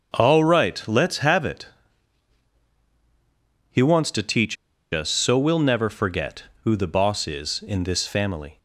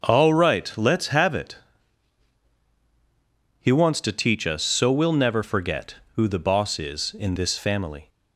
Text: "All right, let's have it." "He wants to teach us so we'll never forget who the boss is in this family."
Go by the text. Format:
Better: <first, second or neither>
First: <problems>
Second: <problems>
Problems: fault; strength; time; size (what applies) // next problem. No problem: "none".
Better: second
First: starts louder than the rest; until 1.2 s; 6.5 dB // pauses between "teach" and "us"; at 4.5 s; 0.37 s long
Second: starts louder than the rest; until 1.0 s; 6.5 dB